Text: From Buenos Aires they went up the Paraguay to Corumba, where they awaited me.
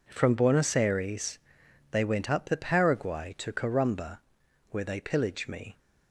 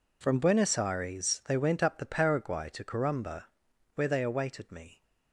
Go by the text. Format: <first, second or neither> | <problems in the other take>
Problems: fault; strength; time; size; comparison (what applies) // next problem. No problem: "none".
second | pauses between "Aires" and "they"; noticeable; at 1.4 s; 0.50 s long // says "pillage" for "awaited"; at 5.0 s